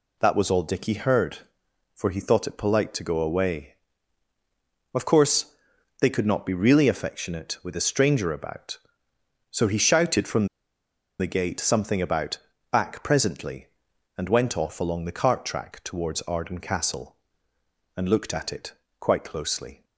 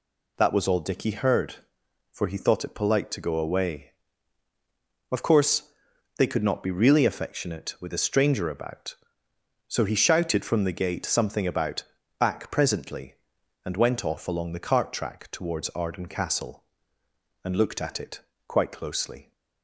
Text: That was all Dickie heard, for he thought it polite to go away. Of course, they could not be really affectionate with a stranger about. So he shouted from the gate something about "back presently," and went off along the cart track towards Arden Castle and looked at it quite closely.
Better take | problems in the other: second | pauses between "from" and "the"; noticeable; at 10.4 s; 0.73 s long // pauses between "about" and "back"; slight; at 12.3 s; 0.34 s long; also in the second // pauses between "it" and "quite"; slight; at 18.7 s; 0.26 s long; slight in the second

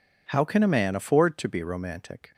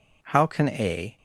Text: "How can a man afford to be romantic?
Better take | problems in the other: first | stops before "man afford to be romantic"; at 1.1 s

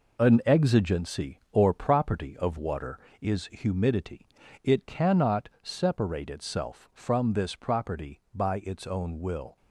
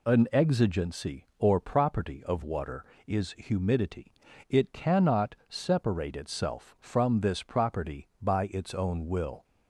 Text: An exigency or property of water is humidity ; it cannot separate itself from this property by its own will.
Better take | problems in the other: second | gets quieter; throughout; 6.5 dB

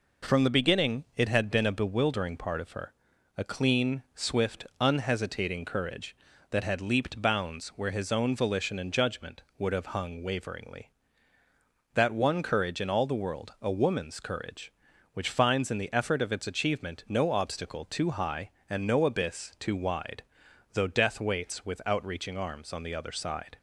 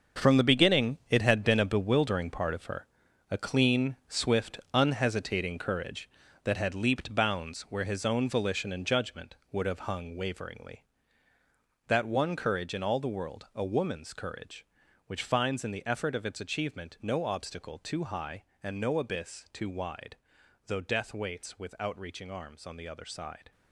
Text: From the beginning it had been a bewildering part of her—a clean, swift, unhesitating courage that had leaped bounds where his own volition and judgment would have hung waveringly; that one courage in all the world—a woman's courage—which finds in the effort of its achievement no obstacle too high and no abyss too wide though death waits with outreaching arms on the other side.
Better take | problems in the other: first | gets quieter; strong; throughout; 11 dB // pauses between "wide" and "though"; noticeable; at 20.1 s; 0.48 s long; noticeable in the first

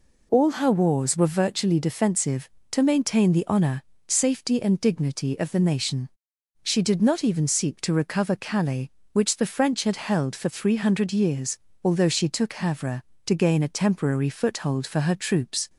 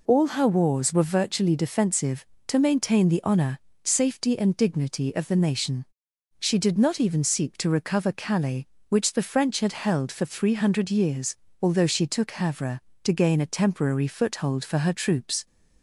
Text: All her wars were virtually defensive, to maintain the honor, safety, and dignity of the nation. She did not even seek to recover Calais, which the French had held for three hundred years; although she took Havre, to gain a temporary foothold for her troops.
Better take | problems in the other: neither | none

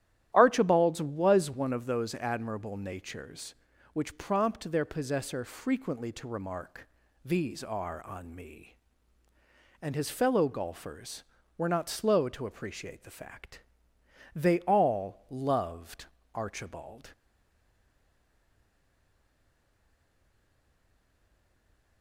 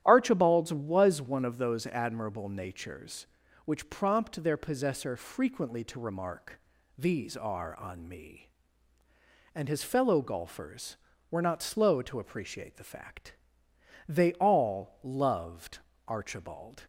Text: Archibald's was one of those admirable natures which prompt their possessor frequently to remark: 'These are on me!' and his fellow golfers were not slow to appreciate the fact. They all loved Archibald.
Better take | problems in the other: second | starts louder than the rest; strong; until 1.3 s; 12 dB; strong in the second // pauses between "loved" and "Archibald"; slight; at 16.0 s; 0.28 s long; slight in the second // stays silent after the last word; strong; from 17.1 s on; 4.9 s long

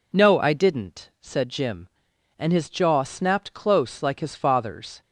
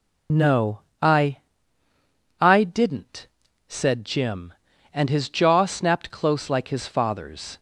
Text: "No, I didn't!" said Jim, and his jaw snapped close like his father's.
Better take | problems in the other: first | says "I" twice; at 2.3 s

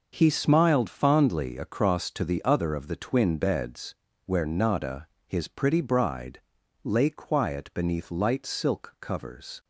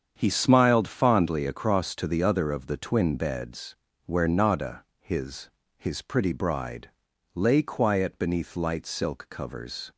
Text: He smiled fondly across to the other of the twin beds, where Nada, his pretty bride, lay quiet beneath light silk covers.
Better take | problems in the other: first | starts louder than the rest; strong; until 1.1 s; 7.5 dB // says "his" twice; at 5.7 s

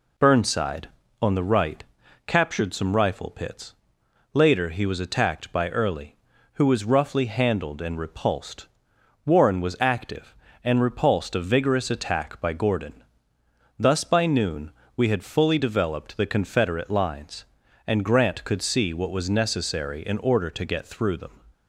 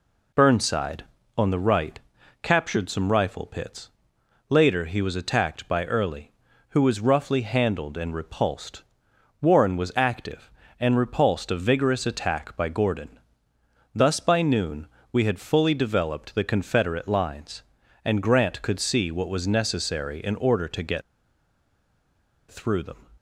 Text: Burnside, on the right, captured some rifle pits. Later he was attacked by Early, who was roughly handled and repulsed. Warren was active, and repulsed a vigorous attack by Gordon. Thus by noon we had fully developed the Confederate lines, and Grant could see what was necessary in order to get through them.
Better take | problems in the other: first | pauses between "noon" and "we"; slight; at 14.8 s; 0.26 s long; slight in the first // pauses between "get" and "through"; strong; at 21.0 s; 1.4 s long

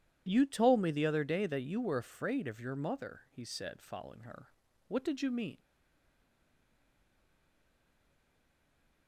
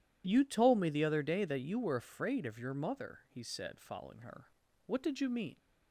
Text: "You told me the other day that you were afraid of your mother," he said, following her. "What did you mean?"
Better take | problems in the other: second | stays silent after the last word; strong; from 5.5 s on; 3.5 s long

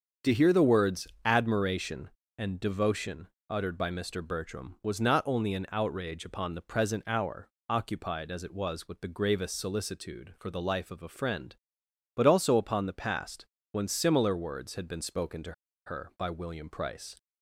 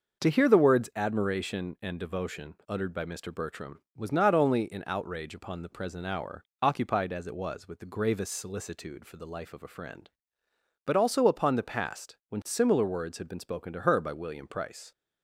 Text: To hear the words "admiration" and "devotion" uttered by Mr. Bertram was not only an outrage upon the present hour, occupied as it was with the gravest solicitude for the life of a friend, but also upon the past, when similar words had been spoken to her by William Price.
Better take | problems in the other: second | starts louder than the rest; strong; until 1.3 s; 7 dB; noticeable in the second // pauses between "words" and "admiration"; slight; at 1.0 s; 0.16 s long // pauses between "devotion" and "uttered"; slight; at 3.2 s; 0.22 s long // pauses between "to" and "her"; slight; at 15.5 s; 0.33 s long

